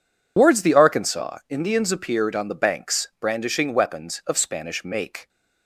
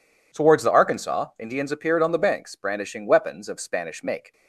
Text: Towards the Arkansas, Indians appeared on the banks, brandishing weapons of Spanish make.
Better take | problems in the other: second | loses the start of "Towards"; at 0.3 s; 135 ms

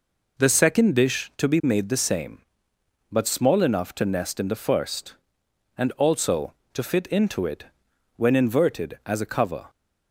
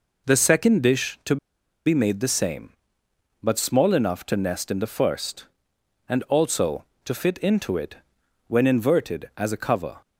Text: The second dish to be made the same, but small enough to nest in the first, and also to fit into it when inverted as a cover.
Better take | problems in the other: first | pauses between "to" and "be"; noticeable; at 1.3 s; 0.49 s long // pauses between "it" and "when"; noticeable; at 7.9 s; 0.50 s long; noticeable in the first

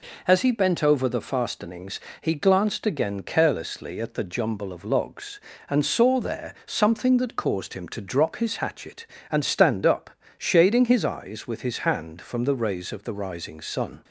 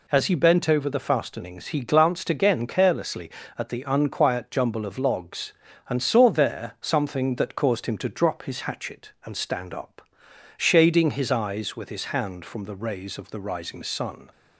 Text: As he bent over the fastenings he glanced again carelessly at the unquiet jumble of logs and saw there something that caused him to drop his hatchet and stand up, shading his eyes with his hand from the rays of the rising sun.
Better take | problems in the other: second | pauses between "fastenings" and "he"; slight; at 1.9 s; 0.20 s long // skips "unquiet"; at 4.2 s

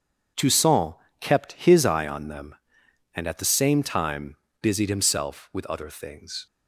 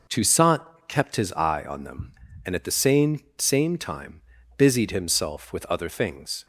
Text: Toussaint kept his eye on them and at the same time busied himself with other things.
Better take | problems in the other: first | pauses between "Toussaint" and "kept"; slight; at 0.6 s; 0.26 s long; slight in the first // says "same" twice; at 3.3 s // pauses between "time" and "busied"; slight; at 4.2 s; 0.34 s long; slight in the first

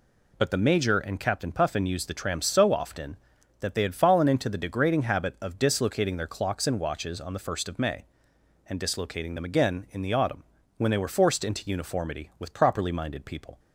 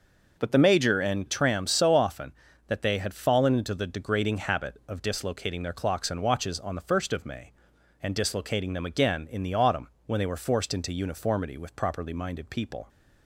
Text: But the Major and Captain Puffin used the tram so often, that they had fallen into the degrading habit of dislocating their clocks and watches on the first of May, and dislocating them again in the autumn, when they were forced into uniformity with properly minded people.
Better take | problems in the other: first | skips "Captain Puffin used the"; at 1.2 s

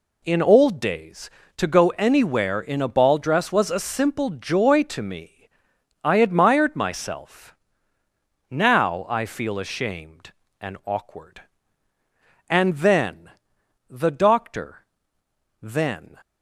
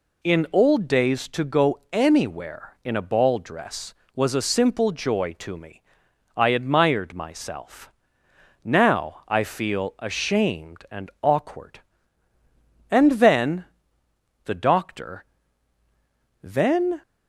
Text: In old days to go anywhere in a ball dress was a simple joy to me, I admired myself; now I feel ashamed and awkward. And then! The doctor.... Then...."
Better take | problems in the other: neither | none

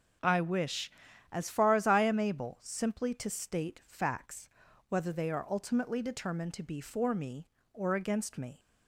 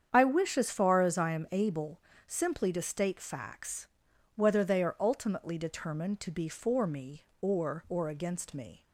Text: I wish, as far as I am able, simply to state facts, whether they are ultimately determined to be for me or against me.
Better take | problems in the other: first | starts louder than the rest; strong; until 1.1 s; 8 dB // says "or" twice; at 7.8 s

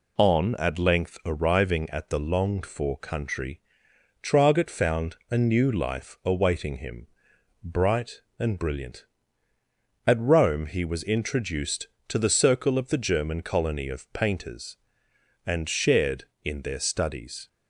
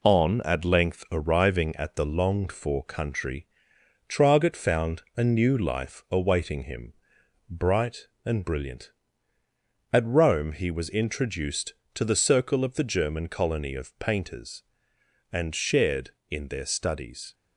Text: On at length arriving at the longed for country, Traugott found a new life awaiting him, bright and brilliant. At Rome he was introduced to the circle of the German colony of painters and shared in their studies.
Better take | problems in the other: first | gets quieter; noticeable; throughout; 4 dB

